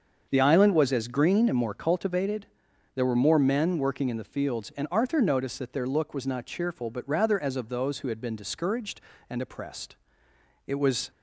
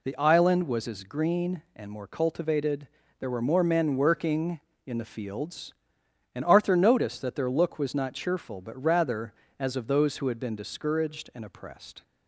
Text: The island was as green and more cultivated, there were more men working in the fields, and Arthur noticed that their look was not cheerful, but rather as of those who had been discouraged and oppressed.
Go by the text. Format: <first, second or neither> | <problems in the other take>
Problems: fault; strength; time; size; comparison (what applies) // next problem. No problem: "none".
second | starts louder than the rest; until 1.3 s; 7 dB // goes on to say "It was"; slight; from 10.6 s on; 0.44 s long